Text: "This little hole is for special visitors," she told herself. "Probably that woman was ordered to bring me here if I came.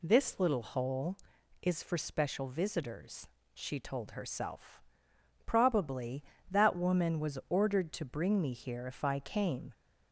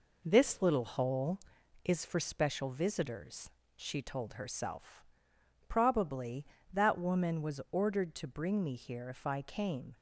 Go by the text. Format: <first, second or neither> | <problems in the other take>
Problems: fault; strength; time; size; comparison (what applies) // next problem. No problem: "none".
first | gets quieter; noticeable; throughout; 4 dB